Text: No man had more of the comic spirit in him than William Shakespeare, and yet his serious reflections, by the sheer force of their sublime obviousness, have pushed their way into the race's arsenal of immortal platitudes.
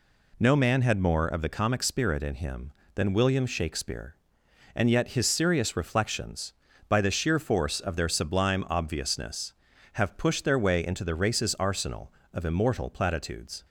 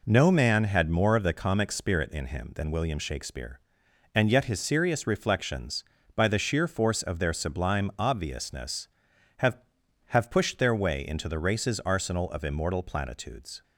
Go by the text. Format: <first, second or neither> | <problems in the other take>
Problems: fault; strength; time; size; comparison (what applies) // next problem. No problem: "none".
first | says "have" twice; at 10.0 s